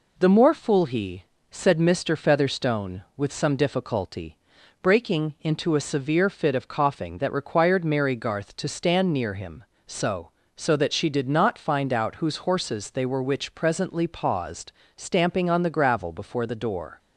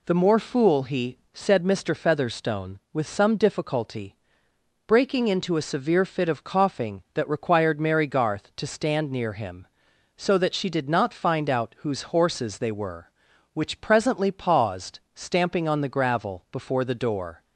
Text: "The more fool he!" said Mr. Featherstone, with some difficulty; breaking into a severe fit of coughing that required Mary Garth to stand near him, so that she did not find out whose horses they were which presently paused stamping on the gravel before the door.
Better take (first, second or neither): second